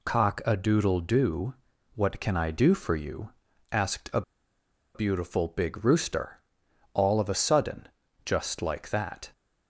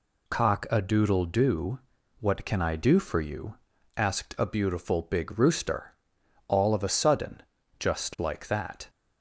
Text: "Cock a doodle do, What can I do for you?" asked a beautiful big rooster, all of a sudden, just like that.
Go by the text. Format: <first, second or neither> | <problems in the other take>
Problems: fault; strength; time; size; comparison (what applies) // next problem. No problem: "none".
second | pauses between "a" and "beautiful"; noticeable; at 4.2 s; 0.73 s long